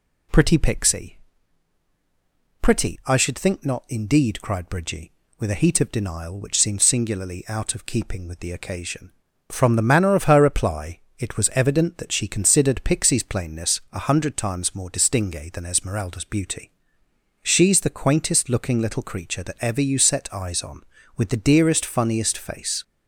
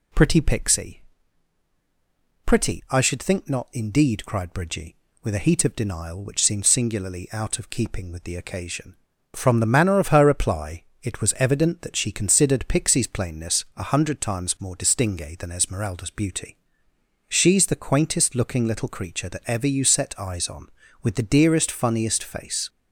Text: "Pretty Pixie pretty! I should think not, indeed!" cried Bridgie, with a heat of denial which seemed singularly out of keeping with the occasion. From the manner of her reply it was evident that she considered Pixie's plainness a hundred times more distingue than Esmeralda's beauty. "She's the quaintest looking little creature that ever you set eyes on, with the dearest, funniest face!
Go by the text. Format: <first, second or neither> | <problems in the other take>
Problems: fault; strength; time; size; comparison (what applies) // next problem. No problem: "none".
neither | pauses between "Pixie" and "pretty"; strong; the same in both // pauses between "reply" and "it"; slight; the same in both